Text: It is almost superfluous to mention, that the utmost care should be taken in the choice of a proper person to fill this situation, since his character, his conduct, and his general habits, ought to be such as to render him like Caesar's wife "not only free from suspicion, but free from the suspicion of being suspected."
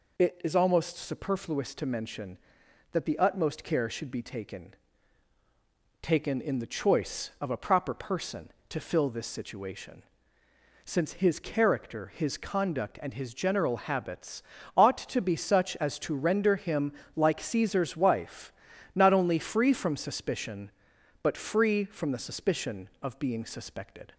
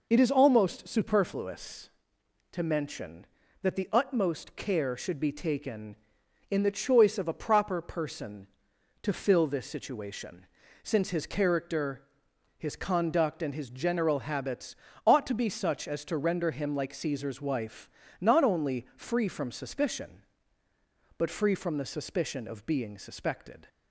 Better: second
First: says "taken" twice; at 6.0 s // pauses between "him" and "like"; slight; at 16.9 s; 0.24 s long // pauses between "wife" and "not"; at 18.5 s; 0.42 s long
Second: pauses between "wife" and "not"; slight; at 17.9 s; 0.30 s long

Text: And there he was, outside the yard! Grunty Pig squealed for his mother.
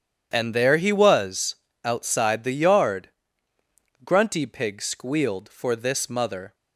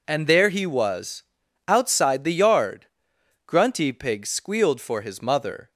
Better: second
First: starts louder than the rest; strong; until 1.3 s; 9 dB // says "this" for "his"; at 5.7 s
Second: none

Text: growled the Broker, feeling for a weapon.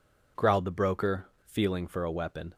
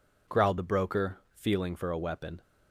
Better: neither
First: none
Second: none

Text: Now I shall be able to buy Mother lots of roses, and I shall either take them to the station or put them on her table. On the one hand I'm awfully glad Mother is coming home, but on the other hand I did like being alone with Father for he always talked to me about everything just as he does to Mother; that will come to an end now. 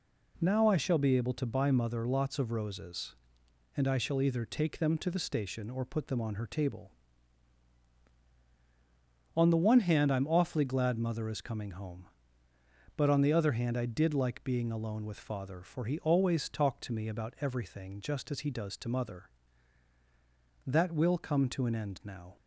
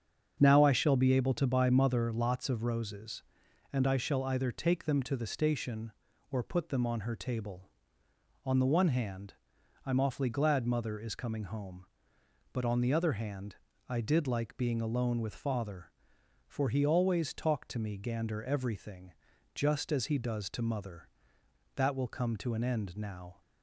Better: first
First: none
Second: starts louder than the rest; until 1.4 s; 7 dB // pauses between "hand" and "I'm"; noticeable; at 9.3 s; 0.52 s long // pauses between "hand" and "I"; slight; at 13.5 s; 0.32 s long // says "gander" for "about"; at 17.9 s // pauses between "everything" and "just"; at 19.1 s; 0.42 s long

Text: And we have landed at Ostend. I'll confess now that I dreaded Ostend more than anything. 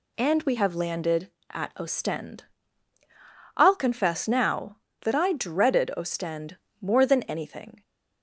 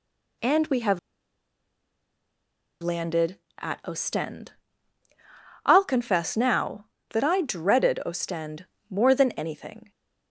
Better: first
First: pauses between "Ostend" and "more"; slight; at 6.5 s; 0.22 s long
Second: pauses between "have" and "landed"; strong; at 0.9 s; 1.8 s long // pauses between "Ostend" and "more"; slight; at 8.6 s; 0.22 s long

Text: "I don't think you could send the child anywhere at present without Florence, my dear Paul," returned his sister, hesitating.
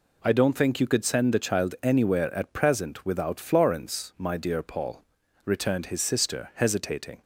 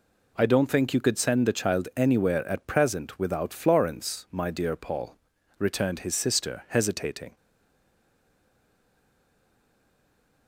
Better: first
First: none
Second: stays silent after the last word; strong; from 7.3 s on; 3.1 s long

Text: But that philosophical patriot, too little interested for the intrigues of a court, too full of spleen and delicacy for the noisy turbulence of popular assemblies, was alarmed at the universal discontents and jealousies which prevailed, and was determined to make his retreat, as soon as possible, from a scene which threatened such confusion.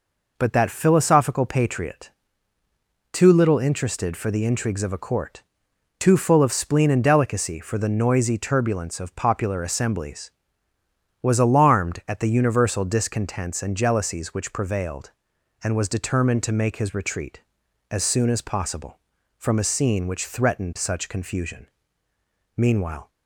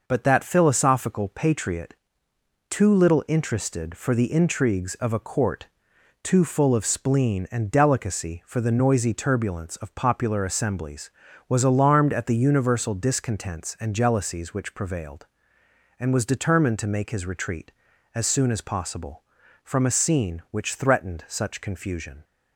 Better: second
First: goes on to say "Meanwhile"; from 22.5 s on; 0.54 s long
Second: none

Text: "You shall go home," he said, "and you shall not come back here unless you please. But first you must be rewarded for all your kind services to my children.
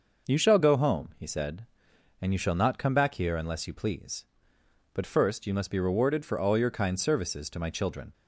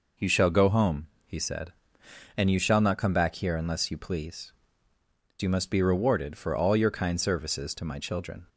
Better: first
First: none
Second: skips "But first"; at 4.9 s

